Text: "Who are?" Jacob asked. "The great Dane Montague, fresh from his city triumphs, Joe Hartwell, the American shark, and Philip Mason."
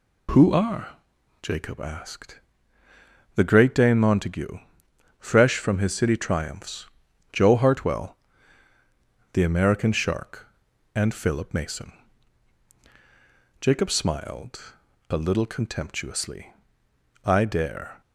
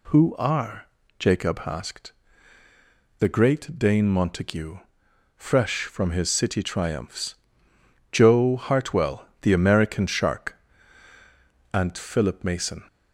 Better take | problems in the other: second | goes on to say "Jacob smiled a little contemptuously I dare"; strong; from 13.6 s on; 4.4 s long

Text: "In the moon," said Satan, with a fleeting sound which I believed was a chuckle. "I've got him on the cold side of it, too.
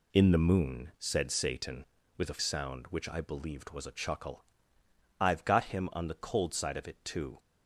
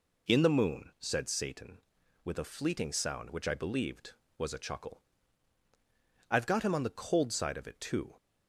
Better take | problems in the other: second | skips "fleeting"; at 2.3 s

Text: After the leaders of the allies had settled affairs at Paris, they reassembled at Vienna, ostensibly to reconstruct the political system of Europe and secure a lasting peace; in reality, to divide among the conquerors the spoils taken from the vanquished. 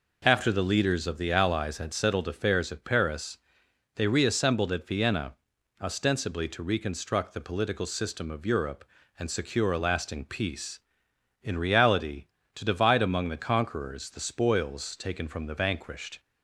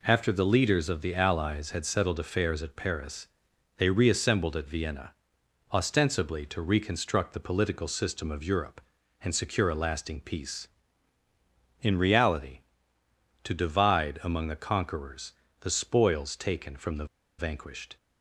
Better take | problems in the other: first | pauses between "conquerors" and "the"; slight; at 15.3 s; 0.26 s long // pauses between "the" and "vanquished"; slight; at 17.0 s; 0.32 s long

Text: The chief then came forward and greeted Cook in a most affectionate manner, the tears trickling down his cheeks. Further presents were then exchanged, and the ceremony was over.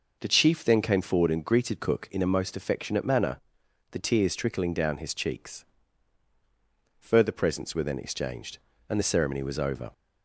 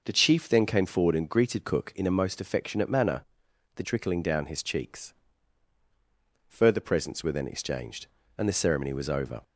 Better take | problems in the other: first | skips "tears"; at 3.8 s

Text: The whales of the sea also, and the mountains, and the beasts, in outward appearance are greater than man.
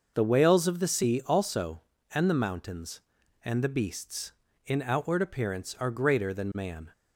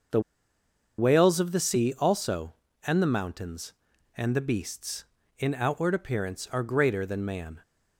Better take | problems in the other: first | pauses between "The" and "whales"; noticeable; at 0.2 s; 0.78 s long

